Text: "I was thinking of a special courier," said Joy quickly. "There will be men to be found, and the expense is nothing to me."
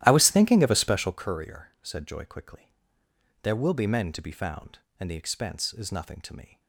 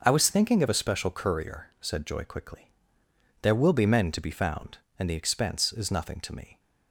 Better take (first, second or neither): second